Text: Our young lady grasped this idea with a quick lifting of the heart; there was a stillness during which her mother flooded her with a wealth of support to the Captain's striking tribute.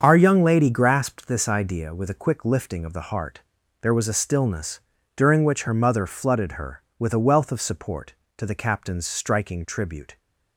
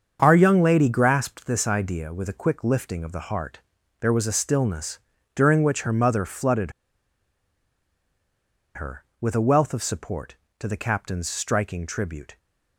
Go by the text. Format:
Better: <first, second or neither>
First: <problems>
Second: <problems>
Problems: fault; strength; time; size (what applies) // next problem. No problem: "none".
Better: first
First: starts louder than the rest; until 1.0 s; 7 dB // pauses between "stillness" and "during"; slight; at 4.7 s; 0.36 s long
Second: starts louder than the rest; until 1.2 s; 7 dB // pauses between "stillness" and "during"; slight; at 4.9 s; 0.36 s long // pauses between "flooded" and "her"; strong; at 6.7 s; 2.0 s long